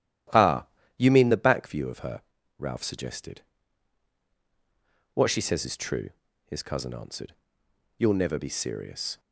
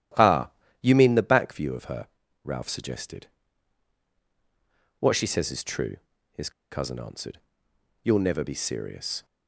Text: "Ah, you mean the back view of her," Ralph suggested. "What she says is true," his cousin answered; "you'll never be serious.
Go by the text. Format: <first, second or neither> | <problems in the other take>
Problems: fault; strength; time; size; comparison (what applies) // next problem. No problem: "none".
first | starts louder than the rest; strong; until 1.4 s; 12 dB; strong in the first // pauses between "his" and "cousin"; slight; at 6.5 s; 0.21 s long